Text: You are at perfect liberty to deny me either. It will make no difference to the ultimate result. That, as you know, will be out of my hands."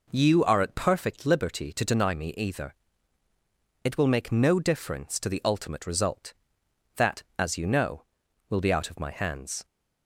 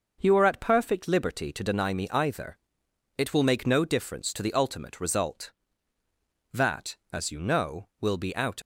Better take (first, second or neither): first